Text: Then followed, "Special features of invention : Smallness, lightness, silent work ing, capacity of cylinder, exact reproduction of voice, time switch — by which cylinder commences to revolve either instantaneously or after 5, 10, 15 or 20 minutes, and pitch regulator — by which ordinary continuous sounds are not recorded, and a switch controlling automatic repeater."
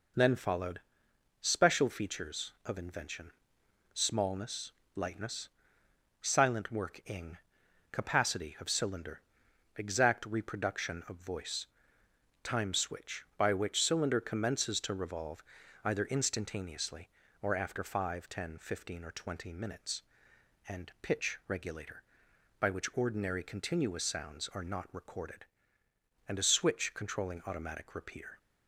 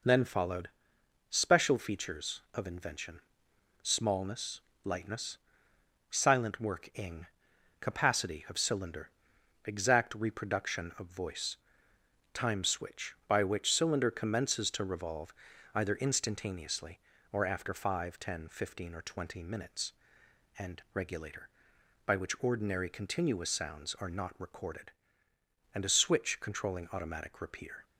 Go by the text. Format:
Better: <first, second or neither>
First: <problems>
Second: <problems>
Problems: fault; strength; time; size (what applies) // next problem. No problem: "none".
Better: first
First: pauses between "revolve" and "either"; at 15.4 s; 0.40 s long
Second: pauses between "revolve" and "either"; at 15.3 s; 0.40 s long // skips "pitch"; at 20.8 s